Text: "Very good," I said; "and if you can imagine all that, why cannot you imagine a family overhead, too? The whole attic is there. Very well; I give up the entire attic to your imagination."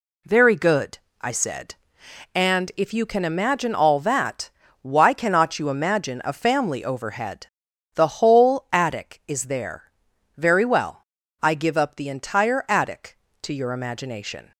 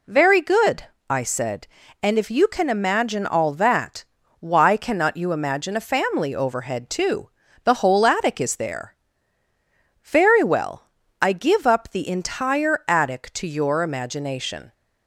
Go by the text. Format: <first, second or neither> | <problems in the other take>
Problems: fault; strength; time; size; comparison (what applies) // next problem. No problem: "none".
second | skips "too"; at 7.7 s